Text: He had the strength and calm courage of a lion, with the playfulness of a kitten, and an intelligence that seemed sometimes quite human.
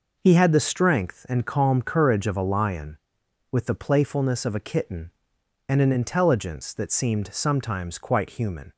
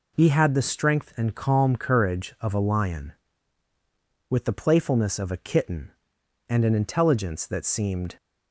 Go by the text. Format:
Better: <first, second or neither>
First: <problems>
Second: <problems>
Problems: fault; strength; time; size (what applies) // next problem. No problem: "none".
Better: first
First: none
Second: stops before "sometimes quite human"; at 8.1 s